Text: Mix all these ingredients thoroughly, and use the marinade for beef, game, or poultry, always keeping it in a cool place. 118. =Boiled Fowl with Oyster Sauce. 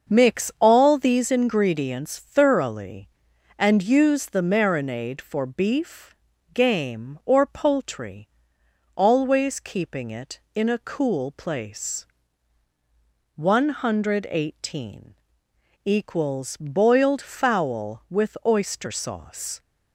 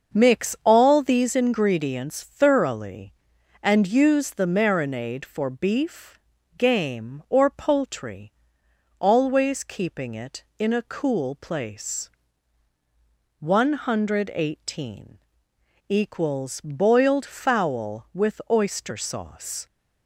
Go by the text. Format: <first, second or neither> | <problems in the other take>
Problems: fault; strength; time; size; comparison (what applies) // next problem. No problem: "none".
neither | starts louder than the rest; the same in both